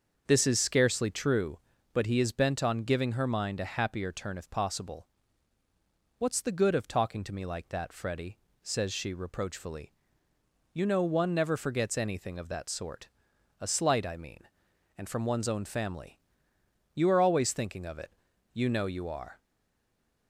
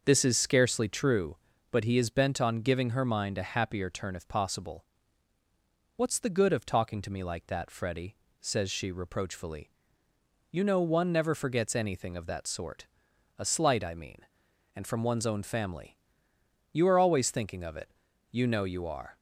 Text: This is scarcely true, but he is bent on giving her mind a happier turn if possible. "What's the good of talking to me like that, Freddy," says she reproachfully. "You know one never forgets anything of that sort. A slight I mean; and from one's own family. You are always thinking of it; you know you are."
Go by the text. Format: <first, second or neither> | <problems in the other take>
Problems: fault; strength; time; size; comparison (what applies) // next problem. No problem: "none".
second | starts louder than the rest; until 1.2 s; 6.5 dB; also in the second // stays silent after the last word; slight; from 19.3 s on; 0.9 s long